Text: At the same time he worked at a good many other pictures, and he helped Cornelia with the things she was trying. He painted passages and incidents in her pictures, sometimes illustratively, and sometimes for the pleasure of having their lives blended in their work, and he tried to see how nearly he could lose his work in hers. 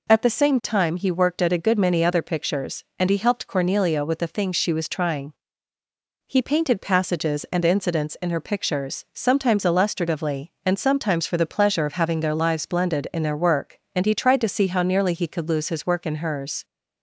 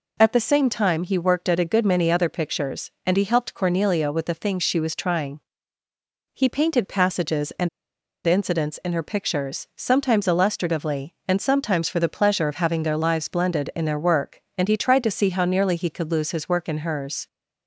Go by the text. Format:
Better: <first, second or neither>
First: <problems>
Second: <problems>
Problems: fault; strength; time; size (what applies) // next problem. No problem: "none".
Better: first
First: none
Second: pauses between "and" and "incidents"; noticeable; at 7.6 s; 0.57 s long